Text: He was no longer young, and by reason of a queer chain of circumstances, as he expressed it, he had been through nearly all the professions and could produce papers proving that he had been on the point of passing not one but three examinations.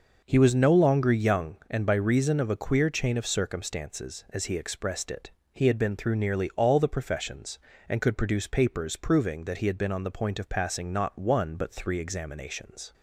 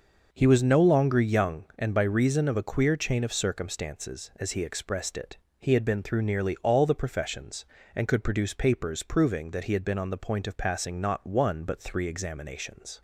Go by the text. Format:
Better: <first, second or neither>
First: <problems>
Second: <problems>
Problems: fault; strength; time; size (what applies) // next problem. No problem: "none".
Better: neither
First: none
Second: none